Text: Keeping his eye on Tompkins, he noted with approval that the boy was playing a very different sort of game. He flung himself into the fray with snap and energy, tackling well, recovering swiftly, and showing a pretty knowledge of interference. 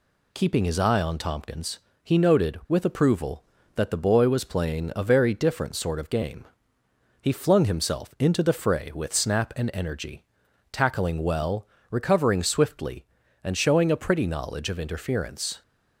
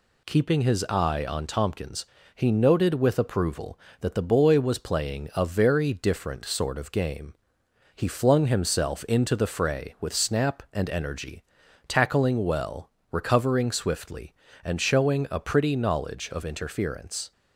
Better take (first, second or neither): neither